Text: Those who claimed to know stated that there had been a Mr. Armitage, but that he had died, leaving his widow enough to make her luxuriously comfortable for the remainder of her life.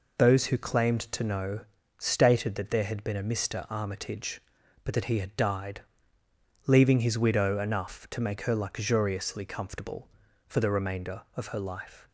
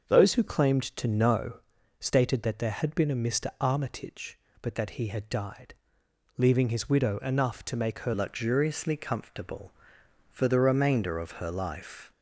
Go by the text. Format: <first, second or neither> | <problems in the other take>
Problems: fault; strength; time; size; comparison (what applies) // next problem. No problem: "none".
first | starts louder than the rest; until 1.2 s; 7 dB // pauses between "know" and "stated"; at 1.5 s; 0.40 s long; also in the first // changes voice at "luxuriously"; from 8.1 s on; 4.0 s long